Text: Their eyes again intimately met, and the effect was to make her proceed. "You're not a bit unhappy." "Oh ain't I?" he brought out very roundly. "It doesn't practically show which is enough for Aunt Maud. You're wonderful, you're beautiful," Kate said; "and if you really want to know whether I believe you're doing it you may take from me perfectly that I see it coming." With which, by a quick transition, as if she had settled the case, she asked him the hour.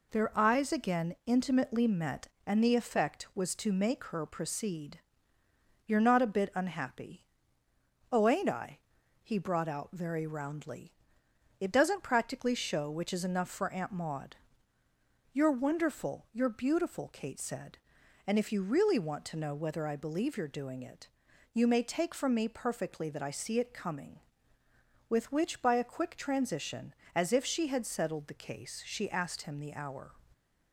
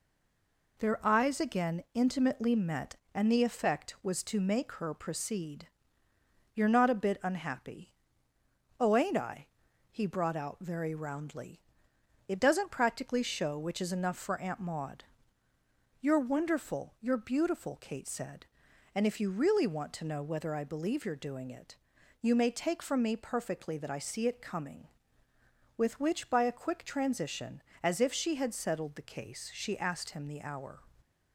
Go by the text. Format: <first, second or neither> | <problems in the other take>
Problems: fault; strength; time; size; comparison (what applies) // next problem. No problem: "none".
first | stays silent before the first word; slight; until 0.7 s; 0.7 s long // pauses between "it" and "you"; at 21.7 s; 0.44 s long; also in the first